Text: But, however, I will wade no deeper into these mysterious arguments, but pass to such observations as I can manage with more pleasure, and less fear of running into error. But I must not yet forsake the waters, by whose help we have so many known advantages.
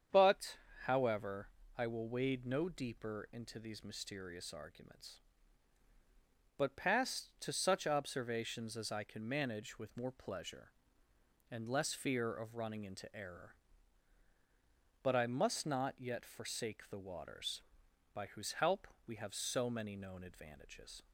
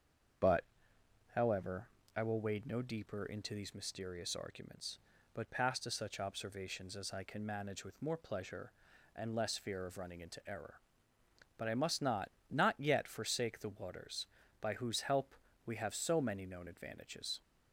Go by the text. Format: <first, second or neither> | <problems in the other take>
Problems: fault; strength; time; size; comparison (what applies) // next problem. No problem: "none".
first | starts louder than the rest; strong; until 2.3 s; 7.5 dB; strong in the first // says "not" twice; at 12.4 s // pauses between "help" and "we"; slight; at 15.3 s; 0.30 s long; slight in the first